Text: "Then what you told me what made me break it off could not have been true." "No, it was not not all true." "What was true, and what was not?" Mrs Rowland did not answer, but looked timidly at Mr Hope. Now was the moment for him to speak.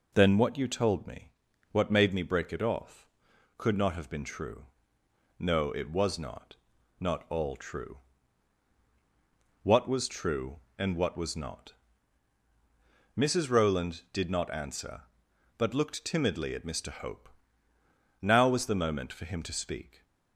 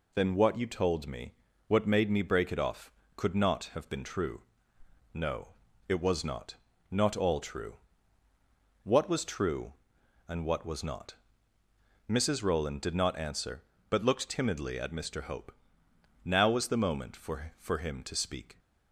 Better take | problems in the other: first | pauses between "me" and "what"; slight; at 1.3 s; 0.34 s long; also in the first // pauses between "not" and "not"; slight; at 6.5 s; 0.34 s long; also in the first // says "for" twice; at 17.5 s

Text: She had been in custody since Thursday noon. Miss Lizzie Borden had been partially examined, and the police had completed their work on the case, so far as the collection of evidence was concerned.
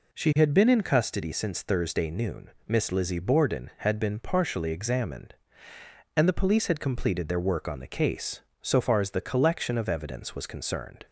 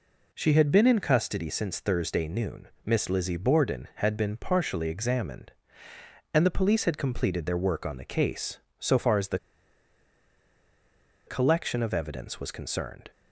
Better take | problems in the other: first | pauses between "the" and "collection"; strong; at 9.3 s; 1.8 s long

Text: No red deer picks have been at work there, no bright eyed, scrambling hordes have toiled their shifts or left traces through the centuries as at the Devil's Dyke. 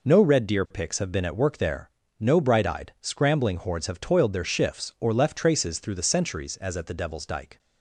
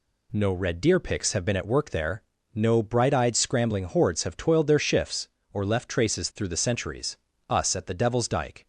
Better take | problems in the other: first | says "us" for "as"; at 7.4 s

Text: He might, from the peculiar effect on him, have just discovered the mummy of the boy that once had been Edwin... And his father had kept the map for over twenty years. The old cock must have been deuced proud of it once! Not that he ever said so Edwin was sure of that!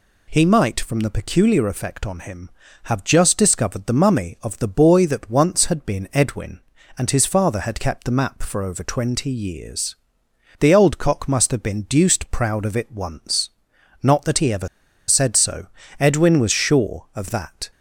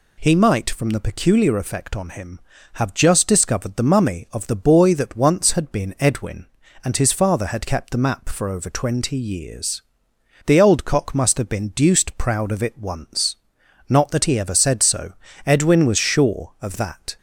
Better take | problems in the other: second | pauses between "ever" and "said"; at 14.6 s; 0.41 s long // pauses between "so" and "Edwin"; slight; at 15.6 s; 0.34 s long; slight in the second

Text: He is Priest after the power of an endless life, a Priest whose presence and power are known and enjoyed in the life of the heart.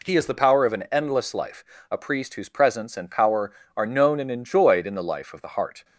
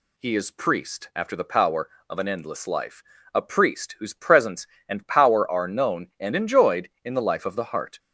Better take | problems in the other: second | skips "Priest after"; at 0.2 s

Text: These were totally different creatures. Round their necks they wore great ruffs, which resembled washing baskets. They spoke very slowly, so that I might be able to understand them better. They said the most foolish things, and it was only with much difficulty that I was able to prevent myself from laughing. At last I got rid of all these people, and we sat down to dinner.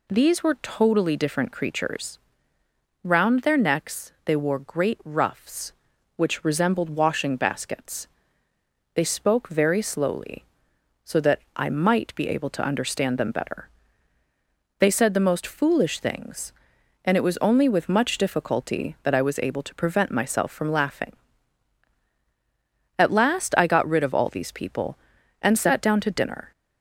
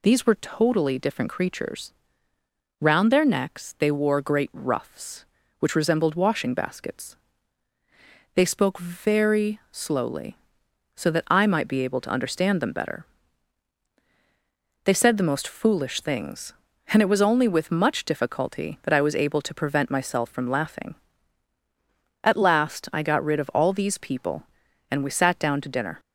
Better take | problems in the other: second | pauses between "that" and "I"; slight; at 11.3 s; 0.16 s long // skips "we"; at 25.5 s

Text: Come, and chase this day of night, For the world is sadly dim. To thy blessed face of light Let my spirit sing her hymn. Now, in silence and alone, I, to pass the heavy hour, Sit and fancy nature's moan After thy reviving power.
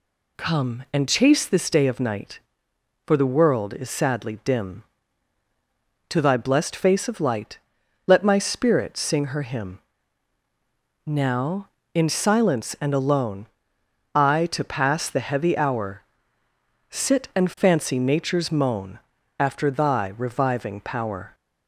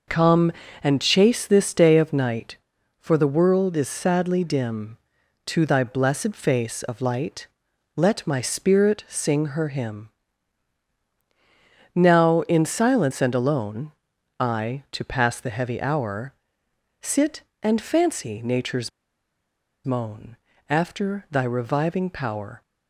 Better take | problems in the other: first | pauses between "light" and "Let"; noticeable; at 7.4 s; 0.48 s long; noticeable in the first // pauses between "nature's" and "moan"; noticeable; at 18.8 s; 0.95 s long // pauses between "moan" and "After"; slight; at 20.3 s; 0.32 s long; also in the first

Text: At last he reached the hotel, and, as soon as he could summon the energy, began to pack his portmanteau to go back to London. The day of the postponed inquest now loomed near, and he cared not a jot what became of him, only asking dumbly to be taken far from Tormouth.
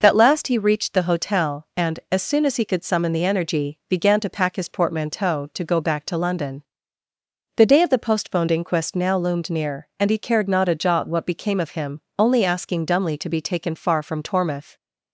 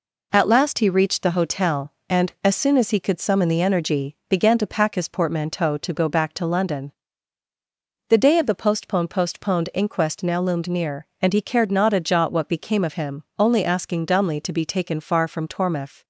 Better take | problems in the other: first | says "postponed" twice; at 9.0 s

